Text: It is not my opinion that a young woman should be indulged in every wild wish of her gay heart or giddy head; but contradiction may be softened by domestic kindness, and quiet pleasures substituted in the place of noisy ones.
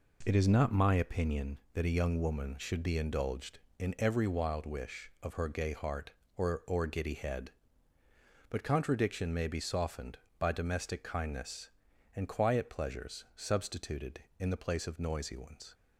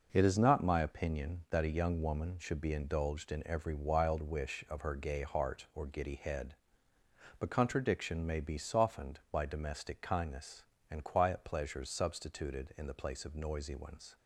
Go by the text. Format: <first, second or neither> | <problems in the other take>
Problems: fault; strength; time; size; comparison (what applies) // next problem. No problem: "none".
second | says "or" twice; at 6.6 s